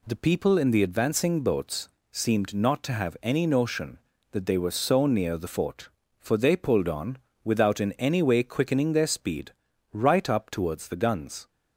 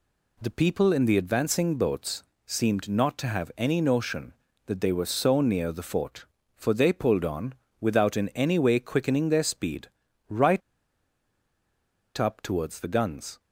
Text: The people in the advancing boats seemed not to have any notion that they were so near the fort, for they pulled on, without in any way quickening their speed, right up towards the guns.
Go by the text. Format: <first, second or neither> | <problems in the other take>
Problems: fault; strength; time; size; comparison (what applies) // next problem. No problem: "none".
first | pauses between "boats" and "seemed"; slight; at 2.2 s; 0.24 s long; slight in the first // pauses between "right" and "up"; strong; at 10.6 s; 1.5 s long